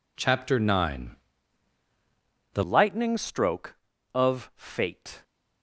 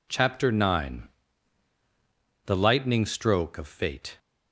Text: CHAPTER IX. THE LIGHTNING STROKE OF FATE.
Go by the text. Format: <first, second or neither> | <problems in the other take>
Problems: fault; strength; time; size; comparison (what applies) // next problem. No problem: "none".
second | changes voice at "LIGHTNING"; from 2.6 s on; 2.6 s long